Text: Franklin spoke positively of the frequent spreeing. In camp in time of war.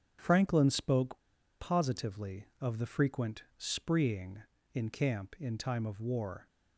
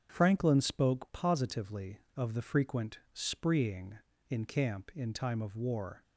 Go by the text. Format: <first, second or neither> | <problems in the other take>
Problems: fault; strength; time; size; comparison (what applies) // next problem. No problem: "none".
second | starts louder than the rest; strong; until 1.2 s; 7 dB; strong in the second // pauses between "spoke" and "positively"; at 1.2 s; 0.38 s long // pauses between "frequent" and "spreeing"; slight; at 3.4 s; 0.16 s long; slight in the second